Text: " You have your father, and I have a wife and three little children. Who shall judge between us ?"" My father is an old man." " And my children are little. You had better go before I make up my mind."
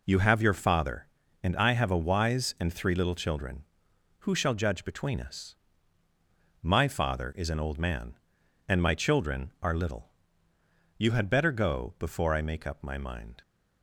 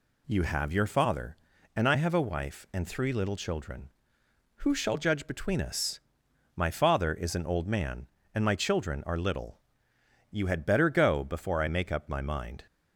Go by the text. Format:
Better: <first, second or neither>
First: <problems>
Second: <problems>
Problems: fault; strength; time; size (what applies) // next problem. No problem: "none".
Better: second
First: says "wise" for "wife"; at 2.0 s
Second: none